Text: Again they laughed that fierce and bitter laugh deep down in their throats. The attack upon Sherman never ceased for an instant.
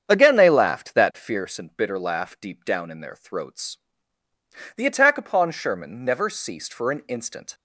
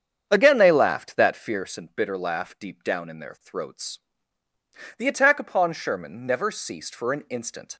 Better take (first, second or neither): neither